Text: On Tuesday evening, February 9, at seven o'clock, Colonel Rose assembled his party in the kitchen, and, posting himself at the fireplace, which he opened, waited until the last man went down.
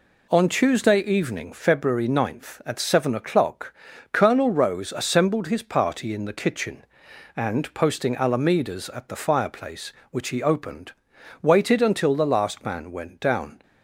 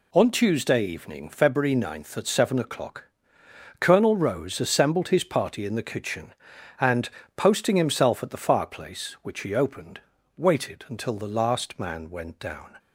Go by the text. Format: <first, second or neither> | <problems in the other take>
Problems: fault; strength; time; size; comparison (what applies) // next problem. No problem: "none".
second | says "alamedas" for "himself"; at 8.1 s